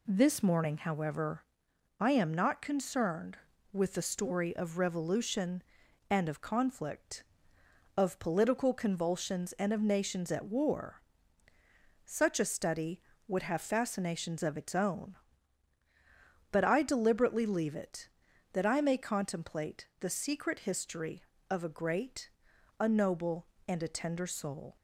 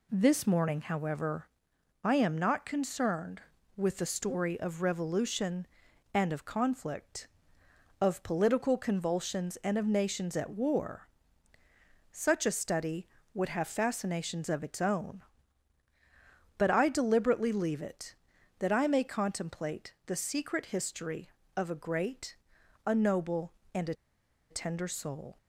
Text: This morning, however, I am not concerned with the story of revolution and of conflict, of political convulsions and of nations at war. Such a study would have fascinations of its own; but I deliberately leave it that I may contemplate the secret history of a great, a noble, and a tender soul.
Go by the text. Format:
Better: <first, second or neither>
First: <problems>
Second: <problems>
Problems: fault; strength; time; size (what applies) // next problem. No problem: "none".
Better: first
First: none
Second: pauses between "a" and "tender"; noticeable; at 23.9 s; 0.56 s long